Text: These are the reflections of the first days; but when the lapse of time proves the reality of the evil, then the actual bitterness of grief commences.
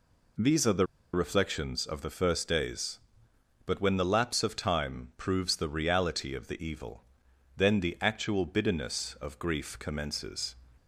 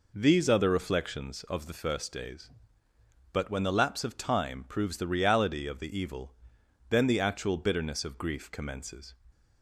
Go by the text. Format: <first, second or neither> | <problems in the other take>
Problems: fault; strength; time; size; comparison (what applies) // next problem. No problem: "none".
second | pauses between "the" and "reflections"; slight; at 0.8 s; 0.28 s long